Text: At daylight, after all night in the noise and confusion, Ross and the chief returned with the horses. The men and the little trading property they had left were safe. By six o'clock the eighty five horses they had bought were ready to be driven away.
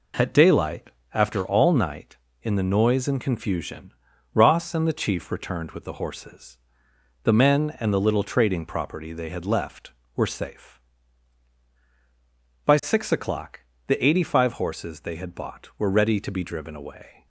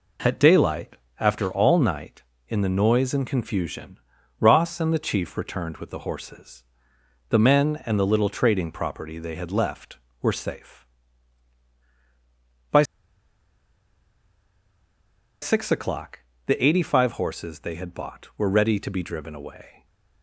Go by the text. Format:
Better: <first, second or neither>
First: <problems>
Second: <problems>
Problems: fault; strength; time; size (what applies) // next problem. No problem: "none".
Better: first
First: pauses between "o'clock" and "the"; slight; at 13.5 s; 0.26 s long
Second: pauses between "By" and "six"; strong; at 12.8 s; 2.5 s long // pauses between "o'clock" and "the"; slight; at 16.1 s; 0.26 s long // stays silent after the last word; slight; from 19.7 s on; 0.5 s long